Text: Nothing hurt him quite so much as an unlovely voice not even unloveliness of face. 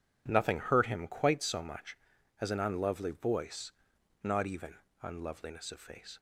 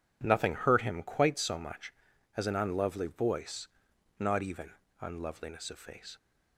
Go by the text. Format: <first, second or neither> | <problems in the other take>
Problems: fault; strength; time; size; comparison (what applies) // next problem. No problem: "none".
neither | pauses between "voice" and "not"; noticeable; the same in both // pauses between "even" and "unloveliness"; slight; the same in both